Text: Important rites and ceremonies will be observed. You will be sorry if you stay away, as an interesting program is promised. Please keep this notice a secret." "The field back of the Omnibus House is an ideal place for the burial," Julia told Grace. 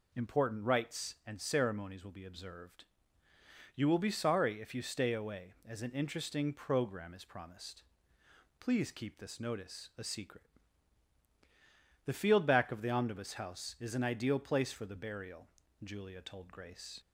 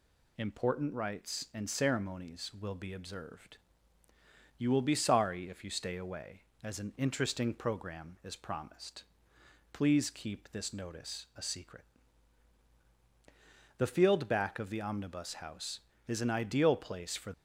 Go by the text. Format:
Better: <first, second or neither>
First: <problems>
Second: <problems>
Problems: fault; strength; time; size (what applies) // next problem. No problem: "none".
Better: first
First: none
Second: stops before "the burial Julia told Grace"; at 17.3 s